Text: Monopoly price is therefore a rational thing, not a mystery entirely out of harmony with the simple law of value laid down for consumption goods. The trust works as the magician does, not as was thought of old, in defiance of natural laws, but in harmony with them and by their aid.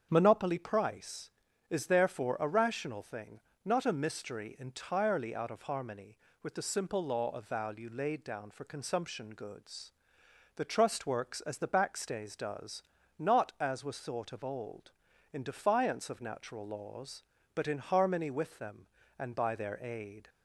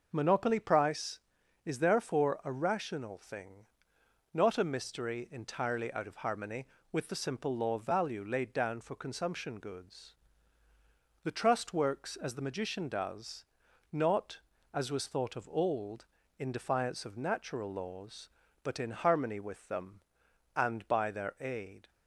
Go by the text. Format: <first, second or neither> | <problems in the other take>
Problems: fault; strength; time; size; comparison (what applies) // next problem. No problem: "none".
second | starts louder than the rest; strong; until 1.1 s; 8 dB // says "backstays" for "magician"; at 11.6 s